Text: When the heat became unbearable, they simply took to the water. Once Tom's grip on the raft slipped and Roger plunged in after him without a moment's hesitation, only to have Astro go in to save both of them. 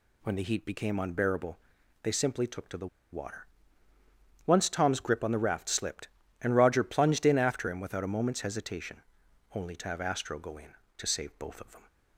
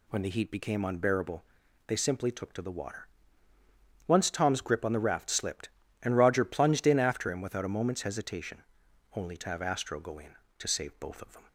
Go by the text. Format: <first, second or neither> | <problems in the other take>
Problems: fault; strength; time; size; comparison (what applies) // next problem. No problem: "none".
second | pauses between "the" and "water"; slight; at 2.8 s; 0.26 s long